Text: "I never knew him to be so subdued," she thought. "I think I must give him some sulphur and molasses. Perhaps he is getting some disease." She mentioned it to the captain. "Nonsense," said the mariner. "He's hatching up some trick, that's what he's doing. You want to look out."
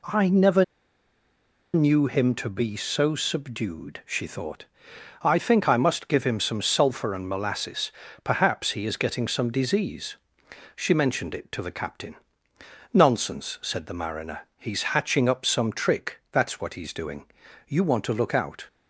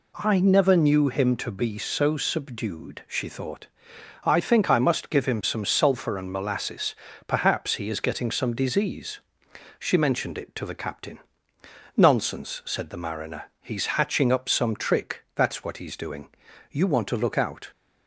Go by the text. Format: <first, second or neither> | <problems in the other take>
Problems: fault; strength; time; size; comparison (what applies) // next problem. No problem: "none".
second | pauses between "never" and "knew"; at 0.6 s; 1.0 s long